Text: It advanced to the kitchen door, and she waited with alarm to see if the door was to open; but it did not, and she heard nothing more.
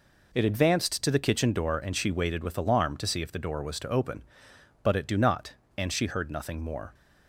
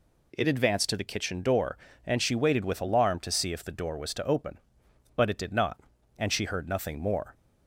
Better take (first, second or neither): second